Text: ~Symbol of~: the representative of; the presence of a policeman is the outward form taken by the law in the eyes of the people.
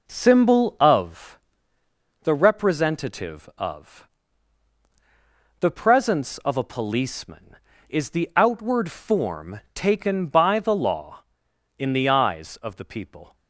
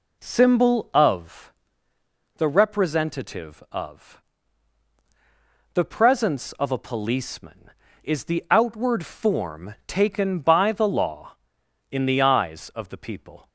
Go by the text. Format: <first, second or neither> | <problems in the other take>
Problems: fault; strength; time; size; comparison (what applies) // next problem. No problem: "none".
second | gets quieter; noticeable; throughout; 5 dB